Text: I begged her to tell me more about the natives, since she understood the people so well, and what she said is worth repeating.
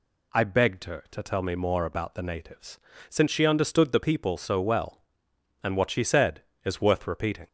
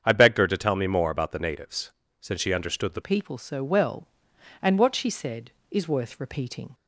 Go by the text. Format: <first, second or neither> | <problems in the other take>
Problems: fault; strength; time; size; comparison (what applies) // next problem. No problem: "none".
first | starts louder than the rest; strong; until 1.0 s; 7.5 dB // changes voice at "people"; from 3.0 s on; 3.7 s long